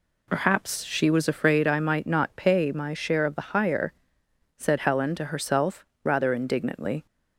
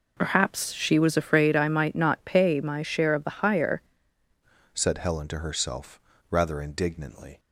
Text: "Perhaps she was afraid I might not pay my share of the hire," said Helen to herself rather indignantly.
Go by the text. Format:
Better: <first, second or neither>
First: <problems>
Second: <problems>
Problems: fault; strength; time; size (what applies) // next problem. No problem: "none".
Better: first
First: pauses between "herself" and "rather"; slight; at 5.8 s; 0.18 s long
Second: changes voice at "said"; from 4.7 s on; 2.6 s long // pauses between "herself" and "rather"; slight; at 5.9 s; 0.32 s long